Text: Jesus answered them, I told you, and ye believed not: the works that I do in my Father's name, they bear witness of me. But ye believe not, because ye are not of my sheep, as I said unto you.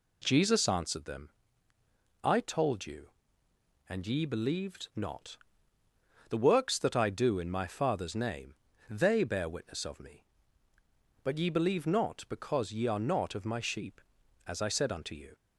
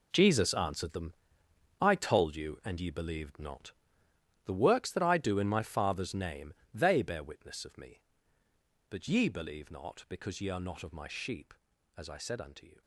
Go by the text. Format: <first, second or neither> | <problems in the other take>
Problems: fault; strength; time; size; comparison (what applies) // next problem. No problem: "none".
first | gets quieter; strong; throughout; 12 dB